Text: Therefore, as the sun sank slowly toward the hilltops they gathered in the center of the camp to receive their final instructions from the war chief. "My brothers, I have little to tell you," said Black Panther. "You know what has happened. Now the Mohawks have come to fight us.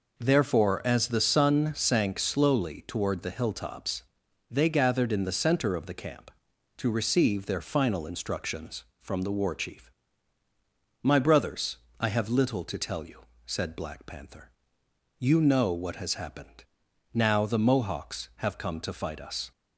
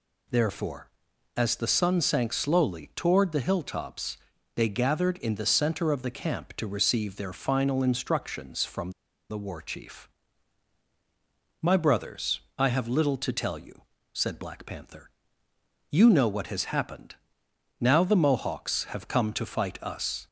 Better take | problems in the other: first | pauses between "hilltops" and "they"; at 4.1 s; 0.38 s long; noticeable in the first // pauses between "from" and "the"; at 8.8 s; 0.40 s long

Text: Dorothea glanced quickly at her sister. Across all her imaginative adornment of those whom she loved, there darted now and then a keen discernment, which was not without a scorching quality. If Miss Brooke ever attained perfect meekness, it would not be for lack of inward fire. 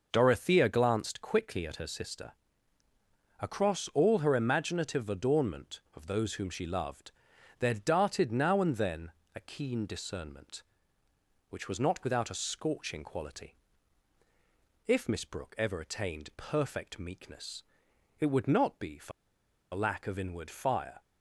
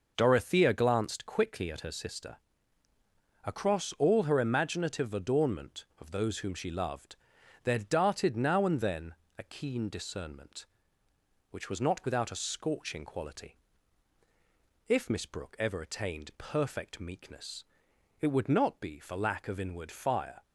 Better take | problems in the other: second | pauses between "then" and "a"; slight; at 9.1 s; 0.22 s long; slight in the second // pauses between "for" and "lack"; noticeable; at 19.1 s; 0.62 s long

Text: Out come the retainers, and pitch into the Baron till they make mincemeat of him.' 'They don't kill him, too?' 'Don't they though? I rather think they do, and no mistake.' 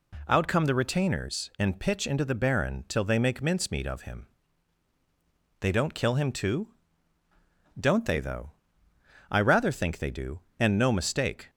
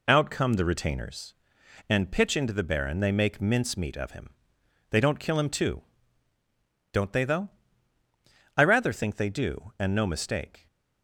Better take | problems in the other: first | skips "till"; at 2.9 s

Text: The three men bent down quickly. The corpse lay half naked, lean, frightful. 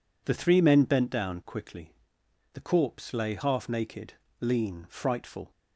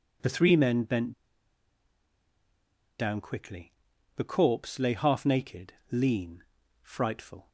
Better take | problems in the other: first | pauses between "bent" and "down"; strong; at 1.1 s; 1.8 s long

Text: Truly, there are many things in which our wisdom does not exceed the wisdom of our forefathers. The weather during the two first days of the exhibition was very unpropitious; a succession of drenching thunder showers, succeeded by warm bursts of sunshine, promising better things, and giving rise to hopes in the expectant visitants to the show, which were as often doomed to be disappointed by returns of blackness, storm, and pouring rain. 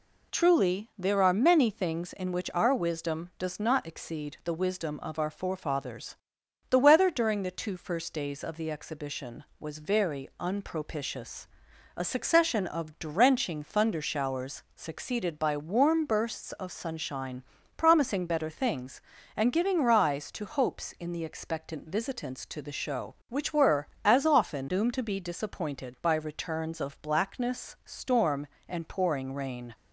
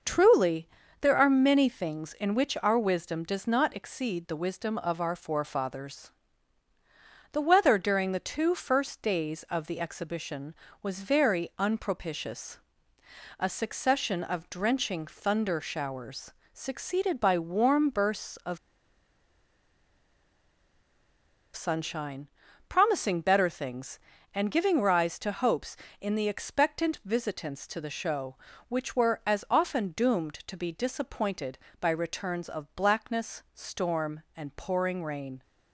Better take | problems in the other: first | pauses between "of" and "sunshine"; strong; at 18.5 s; 2.9 s long

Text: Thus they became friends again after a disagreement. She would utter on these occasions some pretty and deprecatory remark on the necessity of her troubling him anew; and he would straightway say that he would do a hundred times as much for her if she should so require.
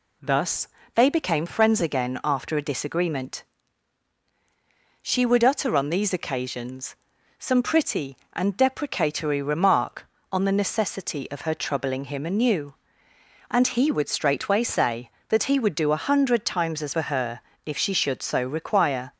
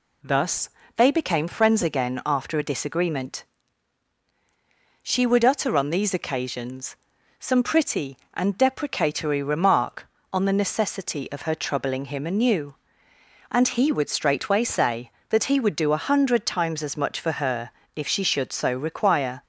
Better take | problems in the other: second | pauses between "Thus" and "they"; slight; at 0.6 s; 0.28 s long; slight in the second // pauses between "occasions" and "some"; at 6.9 s; 0.42 s long; also in the second // skips "much"; at 16.9 s // pauses between "her" and "if"; slight; at 17.4 s; 0.24 s long; slight in the second

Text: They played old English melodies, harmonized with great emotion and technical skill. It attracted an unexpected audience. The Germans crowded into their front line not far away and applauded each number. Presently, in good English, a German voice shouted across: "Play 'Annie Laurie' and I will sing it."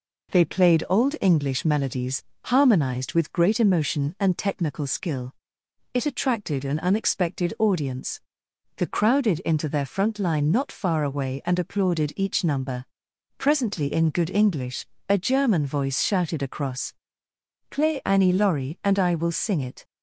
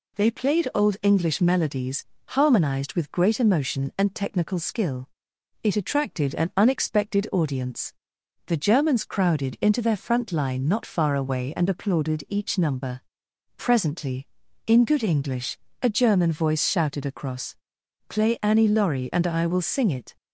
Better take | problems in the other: second | skips "Germans"; at 8.8 s

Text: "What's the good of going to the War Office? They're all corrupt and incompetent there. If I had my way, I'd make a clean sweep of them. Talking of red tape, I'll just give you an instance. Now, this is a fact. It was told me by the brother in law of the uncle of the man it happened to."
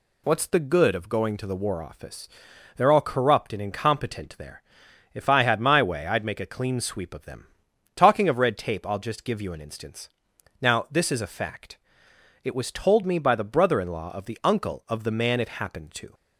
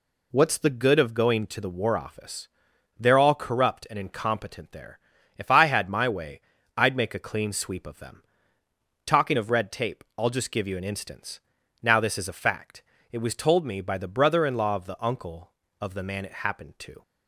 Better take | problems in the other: neither | none

